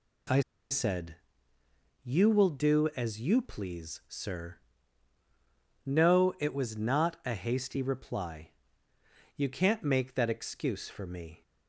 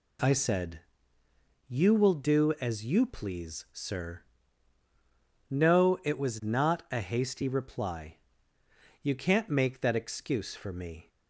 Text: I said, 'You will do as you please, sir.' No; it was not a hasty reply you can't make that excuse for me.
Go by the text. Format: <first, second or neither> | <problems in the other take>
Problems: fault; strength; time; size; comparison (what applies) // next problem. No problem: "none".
second | pauses between "I" and "said"; slight; at 0.4 s; 0.30 s long // pauses between "reply" and "you"; noticeable; at 8.5 s; 0.86 s long; noticeable in the second